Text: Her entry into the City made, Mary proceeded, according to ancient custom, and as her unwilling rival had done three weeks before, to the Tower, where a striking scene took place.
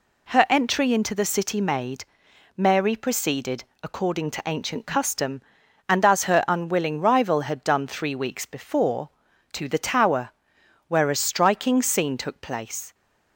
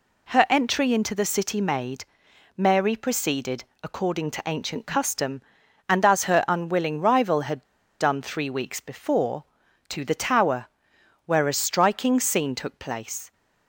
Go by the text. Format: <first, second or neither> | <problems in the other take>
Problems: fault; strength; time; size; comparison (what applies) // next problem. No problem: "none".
first | pauses between "had" and "done"; at 7.6 s; 0.37 s long